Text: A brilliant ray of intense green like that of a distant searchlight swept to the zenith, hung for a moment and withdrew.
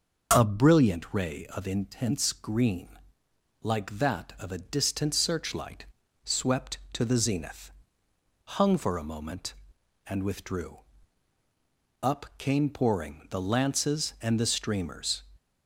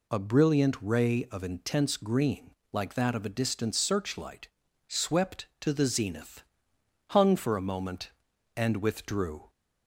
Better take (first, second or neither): second